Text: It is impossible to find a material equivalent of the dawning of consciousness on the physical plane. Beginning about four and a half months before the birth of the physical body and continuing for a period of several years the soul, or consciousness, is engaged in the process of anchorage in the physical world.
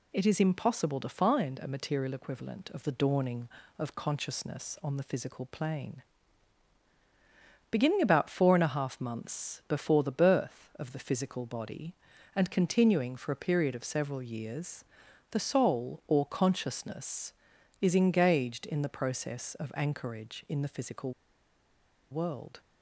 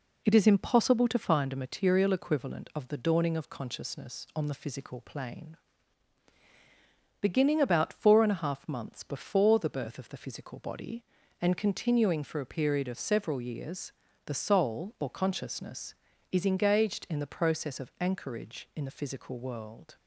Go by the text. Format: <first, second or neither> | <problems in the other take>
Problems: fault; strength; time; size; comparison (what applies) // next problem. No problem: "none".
second | pauses between "years" and "the"; noticeable; at 14.8 s; 0.46 s long; slight in the second // pauses between "physical" and "world"; at 21.1 s; 0.98 s long